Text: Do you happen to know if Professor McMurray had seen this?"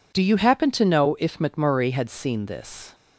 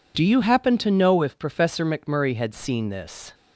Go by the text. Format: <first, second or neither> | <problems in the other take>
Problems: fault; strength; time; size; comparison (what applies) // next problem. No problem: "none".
second | skips "Professor"; at 1.3 s